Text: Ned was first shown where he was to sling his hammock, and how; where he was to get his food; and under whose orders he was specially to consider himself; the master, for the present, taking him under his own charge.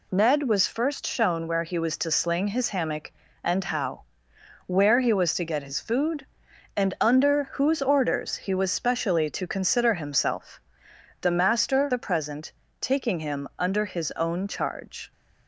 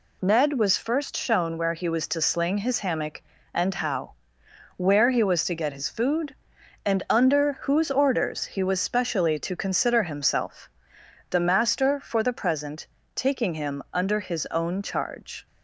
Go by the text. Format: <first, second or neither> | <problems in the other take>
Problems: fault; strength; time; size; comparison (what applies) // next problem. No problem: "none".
second | skips "for"; at 11.9 s